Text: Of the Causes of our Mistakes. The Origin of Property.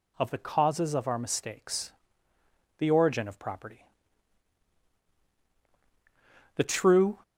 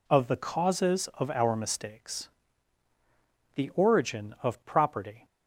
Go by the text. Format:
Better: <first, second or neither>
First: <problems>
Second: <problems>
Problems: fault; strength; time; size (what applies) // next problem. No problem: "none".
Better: second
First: goes on to say "The true"; noticeable; from 6.5 s on; 0.66 s long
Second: none